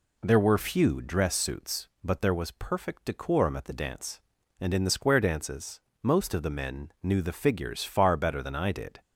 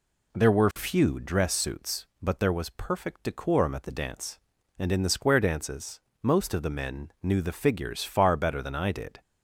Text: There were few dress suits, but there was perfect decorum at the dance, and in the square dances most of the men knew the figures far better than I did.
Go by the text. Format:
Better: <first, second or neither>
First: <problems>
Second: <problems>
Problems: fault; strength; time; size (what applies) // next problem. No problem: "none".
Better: neither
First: pauses between "dances" and "most"; slight; at 5.8 s; 0.22 s long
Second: pauses between "dances" and "most"; slight; at 6.0 s; 0.22 s long